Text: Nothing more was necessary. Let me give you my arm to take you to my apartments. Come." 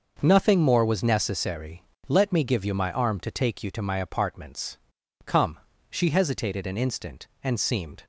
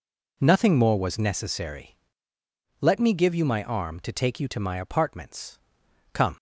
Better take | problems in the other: second | starts louder than the rest; noticeable; until 1.2 s; 6 dB // goes on to say "She hesitated an instant and seemed"; strong; from 5.9 s on; 2.1 s long

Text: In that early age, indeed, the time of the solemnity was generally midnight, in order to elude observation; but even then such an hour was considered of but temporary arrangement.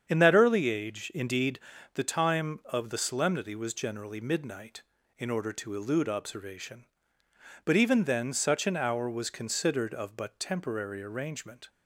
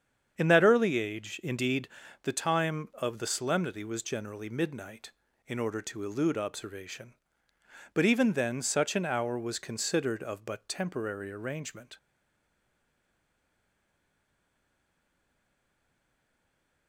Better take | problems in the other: first | starts louder than the rest; strong; until 1.3 s; 8 dB; strong in the first // stays silent after the last word; strong; from 11.9 s on; 4.9 s long

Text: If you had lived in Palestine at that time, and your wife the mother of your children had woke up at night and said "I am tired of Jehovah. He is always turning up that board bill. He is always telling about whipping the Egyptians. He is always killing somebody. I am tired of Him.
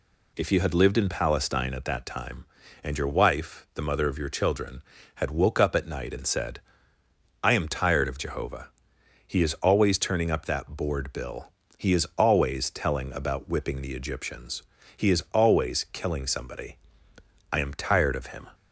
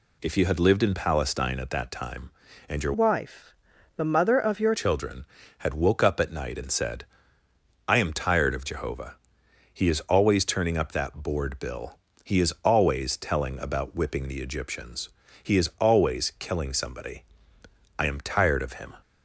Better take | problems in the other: first | changes voice from "wife" to "your"; from 2.9 to 4.7 s; 1.8 s long // pauses between "wife" and "the"; at 3.5 s; 0.42 s long // pauses between "said" and "I"; noticeable; at 7.0 s; 0.84 s long; noticeable in the first

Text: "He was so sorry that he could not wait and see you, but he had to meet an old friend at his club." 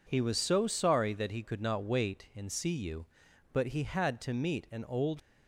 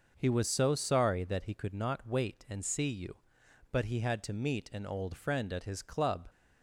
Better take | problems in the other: second | stops before "friend at his club"; at 5.1 s

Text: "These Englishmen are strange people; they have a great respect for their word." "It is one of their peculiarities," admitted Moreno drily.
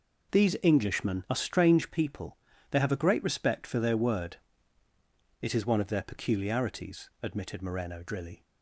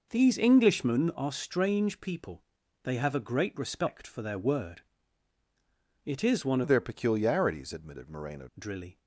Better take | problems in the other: first | changes voice from "of" to "Moreno"; from 6.6 to 8.4 s; 1.8 s long

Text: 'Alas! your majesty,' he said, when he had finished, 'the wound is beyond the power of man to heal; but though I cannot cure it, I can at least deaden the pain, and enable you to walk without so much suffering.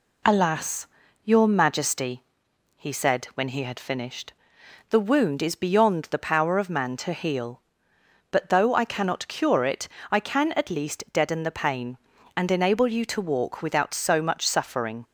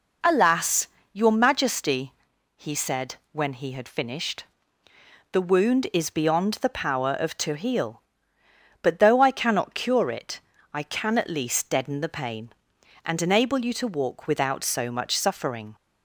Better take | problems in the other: first | skips "man"; at 7.3 s

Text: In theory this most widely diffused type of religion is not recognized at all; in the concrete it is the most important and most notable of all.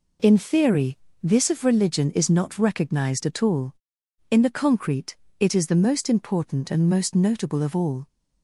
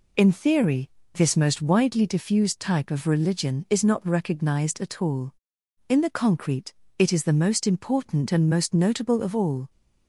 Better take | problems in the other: second | pauses between "theory" and "this"; slight; at 0.9 s; 0.24 s long; slight in the second // skips "most widely diffused type"; at 1.4 s // pauses between "concrete" and "it"; slight; at 5.1 s; 0.24 s long; slight in the second

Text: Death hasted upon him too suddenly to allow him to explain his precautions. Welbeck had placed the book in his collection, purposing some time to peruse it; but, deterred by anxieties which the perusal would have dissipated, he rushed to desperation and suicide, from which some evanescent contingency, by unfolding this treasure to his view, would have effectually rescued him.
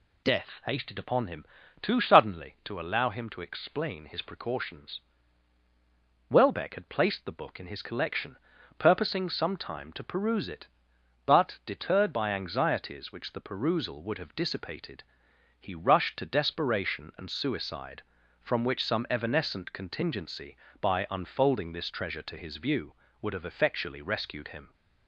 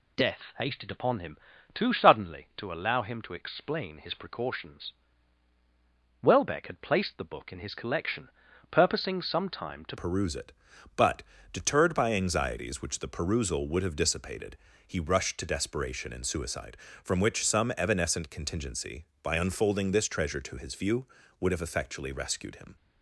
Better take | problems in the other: first | pauses between "him" and "too"; slight; at 1.3 s; 0.36 s long; slight in the first // changes voice at "peruse"; from 9.9 s on; 12.8 s long

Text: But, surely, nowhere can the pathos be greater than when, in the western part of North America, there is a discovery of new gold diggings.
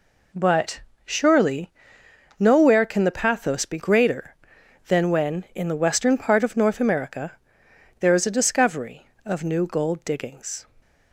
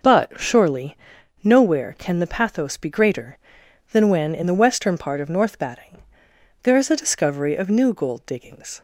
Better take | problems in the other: first | says "Batting" for "America"; at 5.5 s

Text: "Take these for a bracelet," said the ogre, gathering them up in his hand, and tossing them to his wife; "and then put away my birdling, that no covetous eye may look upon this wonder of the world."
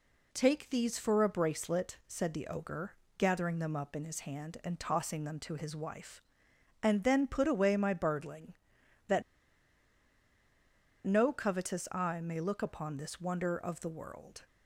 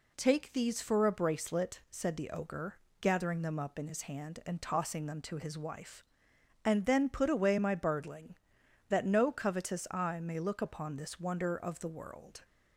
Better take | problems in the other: second | pauses between "that" and "no"; strong; at 9.2 s; 1.8 s long

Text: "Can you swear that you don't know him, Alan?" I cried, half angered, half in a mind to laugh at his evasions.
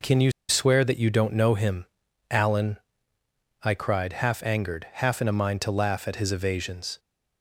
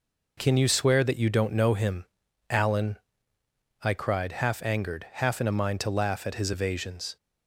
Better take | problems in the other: second | pauses between "you" and "swear"; slight; at 0.3 s; 0.17 s long

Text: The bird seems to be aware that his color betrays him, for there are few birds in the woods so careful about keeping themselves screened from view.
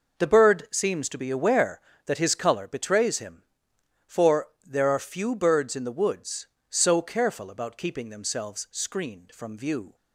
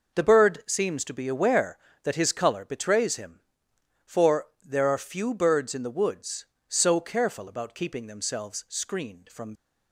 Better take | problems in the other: first | pauses between "for" and "there"; slight; at 4.4 s; 0.16 s long; slight in the first // stops before "view"; at 9.5 s

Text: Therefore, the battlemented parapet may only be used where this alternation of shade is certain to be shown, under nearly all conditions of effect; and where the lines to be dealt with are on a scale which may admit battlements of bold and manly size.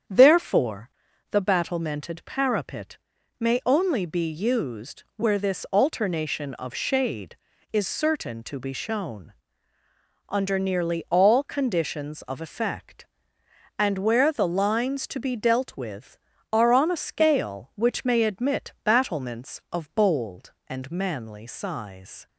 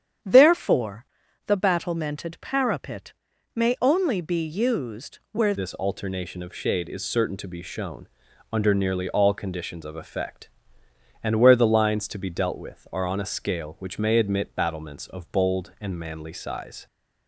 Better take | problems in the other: first | starts louder than the rest; strong; until 1.6 s; 9 dB; strong in the first // pauses between "parapet" and "may"; at 3.1 s; 0.44 s long; also in the first // changes voice at "this"; from 5.5 s on; 11.3 s long

